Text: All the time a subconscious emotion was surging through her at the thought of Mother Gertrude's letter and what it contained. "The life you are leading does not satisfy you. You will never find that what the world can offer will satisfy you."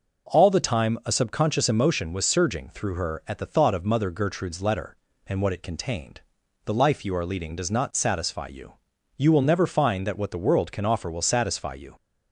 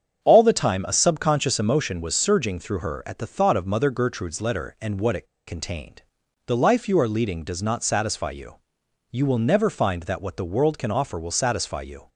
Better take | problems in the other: first | starts louder than the rest; strong; until 1.2 s; 7.5 dB // pauses between "it" and "contained"; slight; at 5.2 s; 0.21 s long

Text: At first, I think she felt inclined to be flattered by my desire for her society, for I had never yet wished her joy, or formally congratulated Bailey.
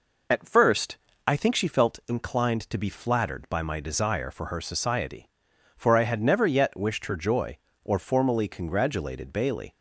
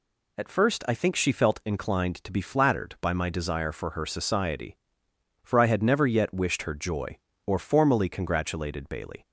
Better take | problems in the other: second | starts louder than the rest; noticeable; until 2.0 s; 5 dB

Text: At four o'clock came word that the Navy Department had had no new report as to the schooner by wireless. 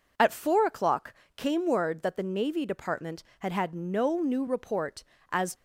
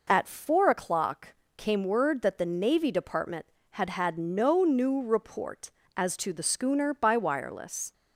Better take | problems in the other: second | pauses between "o'clock" and "came"; slight; at 1.1 s; 0.22 s long; slight in the second // stops before "to the schooner by wireless"; at 5.5 s

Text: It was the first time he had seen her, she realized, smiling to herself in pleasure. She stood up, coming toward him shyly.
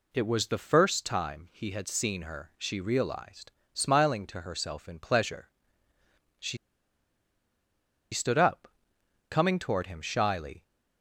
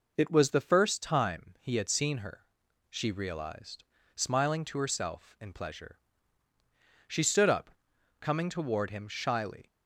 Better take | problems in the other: second | pauses between "She" and "stood"; strong; at 6.5 s; 1.5 s long

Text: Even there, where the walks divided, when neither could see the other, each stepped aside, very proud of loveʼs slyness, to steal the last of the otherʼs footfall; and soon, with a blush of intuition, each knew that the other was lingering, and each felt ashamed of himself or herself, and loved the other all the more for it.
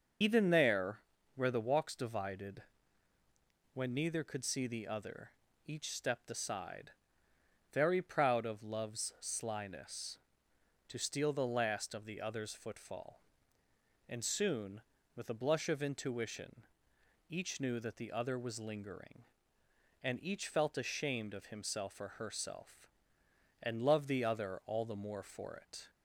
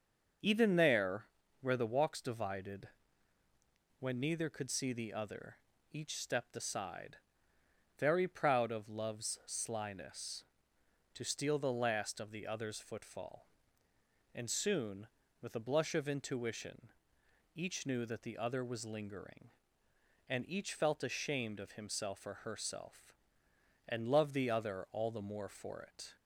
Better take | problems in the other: second | loses the start of "Even"; at 0.2 s; 50 ms // starts louder than the rest; until 1.5 s; 6.5 dB; also in the second

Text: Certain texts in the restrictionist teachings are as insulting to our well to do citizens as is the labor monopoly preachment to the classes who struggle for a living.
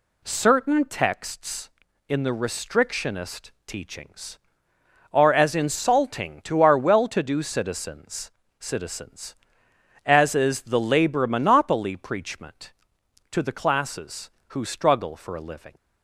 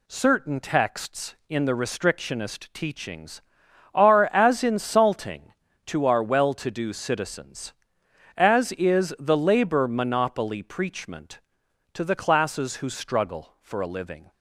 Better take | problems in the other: second | pauses between "restrictionist" and "teachings"; slight; at 3.4 s; 0.16 s long // says "citizens" twice; at 8.5 s

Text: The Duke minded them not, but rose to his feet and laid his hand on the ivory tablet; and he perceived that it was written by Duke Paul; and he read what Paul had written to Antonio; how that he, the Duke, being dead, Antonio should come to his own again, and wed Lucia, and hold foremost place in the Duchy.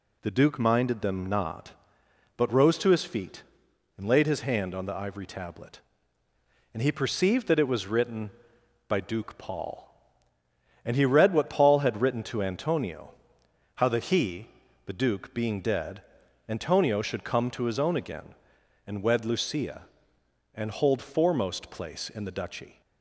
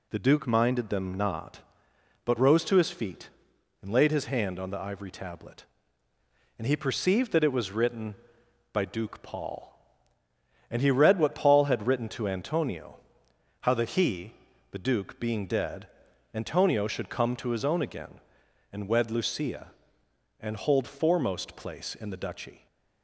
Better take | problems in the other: neither | none

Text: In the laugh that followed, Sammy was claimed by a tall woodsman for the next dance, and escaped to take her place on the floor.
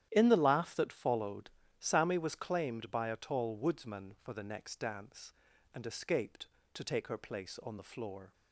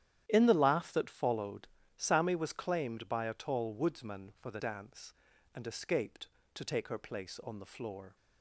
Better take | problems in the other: first | starts louder than the rest; strong; until 1.2 s; 11 dB; strong in the first // skips "next"; at 4.5 s

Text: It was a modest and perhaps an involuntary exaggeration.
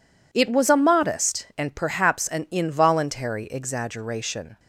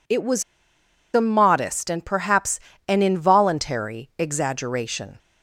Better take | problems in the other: first | pauses between "was" and "a"; noticeable; at 0.4 s; 0.71 s long // pauses between "perhaps" and "an"; slight; at 2.6 s; 0.26 s long

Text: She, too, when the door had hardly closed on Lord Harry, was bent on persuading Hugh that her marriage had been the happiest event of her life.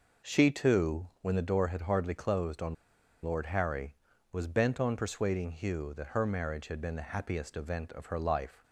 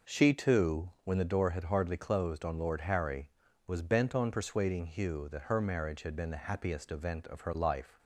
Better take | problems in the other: second | pauses between "on" and "Lord"; noticeable; at 2.7 s; 0.49 s long

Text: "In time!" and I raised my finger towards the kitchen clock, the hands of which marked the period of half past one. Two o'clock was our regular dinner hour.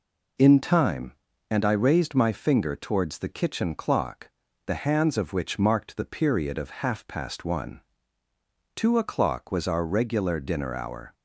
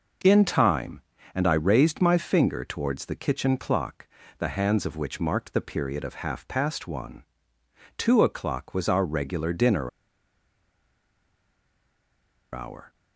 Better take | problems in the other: first | pauses between "dinner" and "hour"; strong; at 9.8 s; 2.6 s long

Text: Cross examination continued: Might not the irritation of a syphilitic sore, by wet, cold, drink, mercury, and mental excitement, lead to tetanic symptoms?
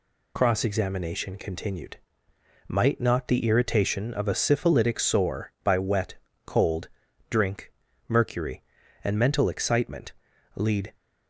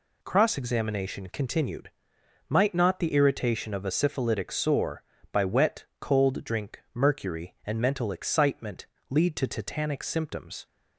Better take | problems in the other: second | stops before "to tetanic symptoms"; at 10.9 s

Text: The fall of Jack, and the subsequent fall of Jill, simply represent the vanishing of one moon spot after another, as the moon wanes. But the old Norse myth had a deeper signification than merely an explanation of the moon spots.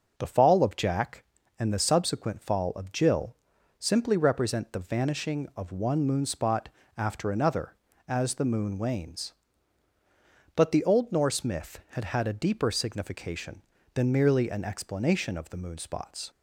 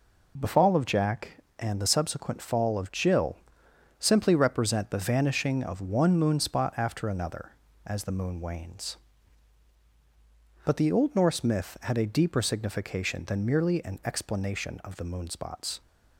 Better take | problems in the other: second | starts louder than the rest; until 1.1 s; 6.5 dB // pauses between "spot" and "after"; slight; at 6.6 s; 0.26 s long // says "had" twice; at 12.0 s

